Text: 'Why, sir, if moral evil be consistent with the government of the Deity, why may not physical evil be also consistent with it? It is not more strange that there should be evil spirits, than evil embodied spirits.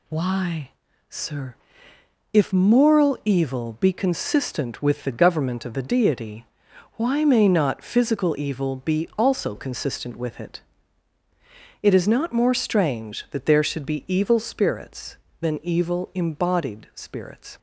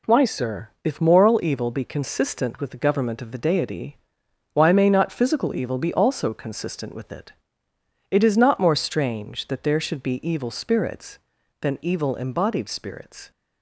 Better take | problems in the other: neither | none

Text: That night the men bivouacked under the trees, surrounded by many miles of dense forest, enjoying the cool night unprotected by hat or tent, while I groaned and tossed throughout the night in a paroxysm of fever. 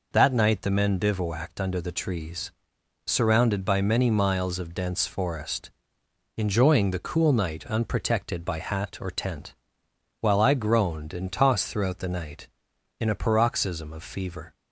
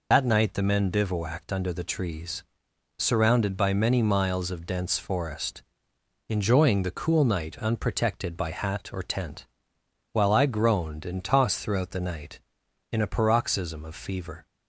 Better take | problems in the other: first | loses the start of "That"; at 0.1 s; 55 ms

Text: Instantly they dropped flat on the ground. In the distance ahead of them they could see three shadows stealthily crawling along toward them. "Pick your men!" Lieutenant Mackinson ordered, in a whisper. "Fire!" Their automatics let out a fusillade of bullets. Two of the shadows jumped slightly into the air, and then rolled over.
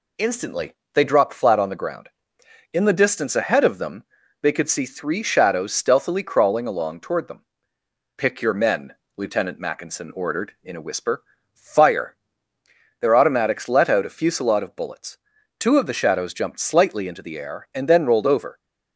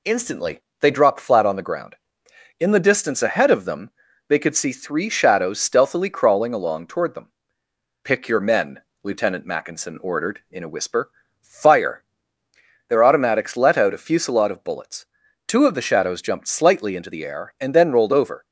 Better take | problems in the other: neither | pauses between "Instantly" and "they"; slight; the same in both // pauses between "them" and "they"; the same in both

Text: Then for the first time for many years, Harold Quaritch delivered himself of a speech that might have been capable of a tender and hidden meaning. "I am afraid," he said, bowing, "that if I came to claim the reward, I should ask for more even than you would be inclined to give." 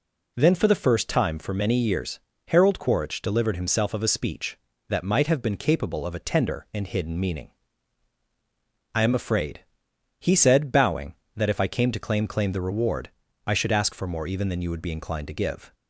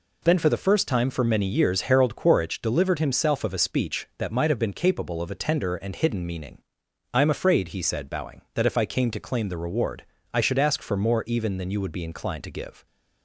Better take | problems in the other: second | says "claim" twice; at 12.2 s

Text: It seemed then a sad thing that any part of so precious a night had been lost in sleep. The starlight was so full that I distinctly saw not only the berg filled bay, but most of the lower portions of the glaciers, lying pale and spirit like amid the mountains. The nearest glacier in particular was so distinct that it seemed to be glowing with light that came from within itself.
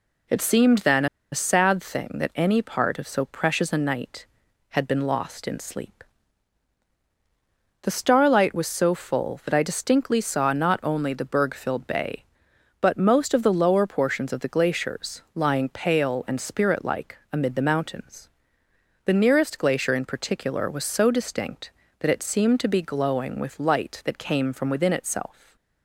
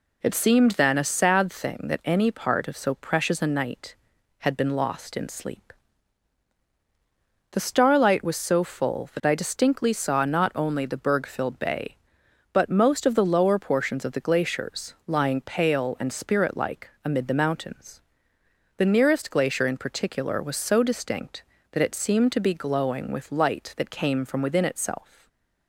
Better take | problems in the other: second | pauses between "then" and "a"; slight; at 1.0 s; 0.26 s long // stays silent after the last word; slight; from 25.3 s on; 0.5 s long; slight in the second

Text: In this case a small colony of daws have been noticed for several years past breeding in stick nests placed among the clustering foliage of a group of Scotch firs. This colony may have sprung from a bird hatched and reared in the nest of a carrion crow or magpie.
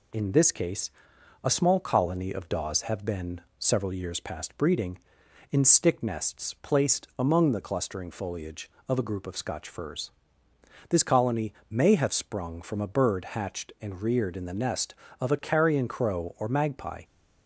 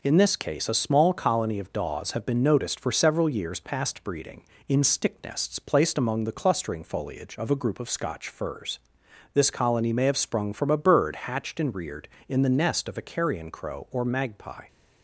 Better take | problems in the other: second | pauses between "case" and "a"; noticeable; at 0.9 s; 0.52 s long // skips "noticed for"; at 3.4 s // pauses between "colony" and "may"; slight; at 11.5 s; 0.16 s long

